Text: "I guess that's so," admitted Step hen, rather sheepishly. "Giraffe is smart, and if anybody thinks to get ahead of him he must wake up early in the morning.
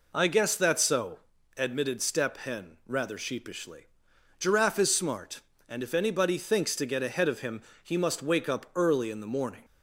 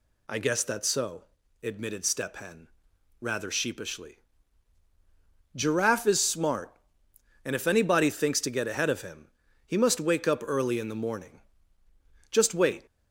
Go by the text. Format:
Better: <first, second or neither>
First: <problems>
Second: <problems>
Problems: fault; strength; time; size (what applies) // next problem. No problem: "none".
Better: first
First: pauses between "him" and "he"; slight; at 7.6 s; 0.22 s long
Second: pauses between "him" and "he"; at 9.2 s; 0.38 s long // goes on to say "Just wait"; from 12.3 s on; 0.54 s long